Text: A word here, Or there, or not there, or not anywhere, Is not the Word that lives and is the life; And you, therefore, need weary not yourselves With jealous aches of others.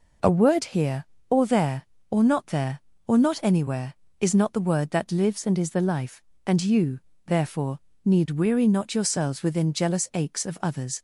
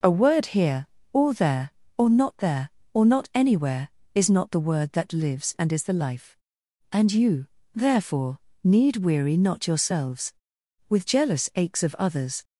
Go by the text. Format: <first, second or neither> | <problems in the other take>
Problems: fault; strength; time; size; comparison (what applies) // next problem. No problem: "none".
second | says "Within" for "With"; at 9.4 s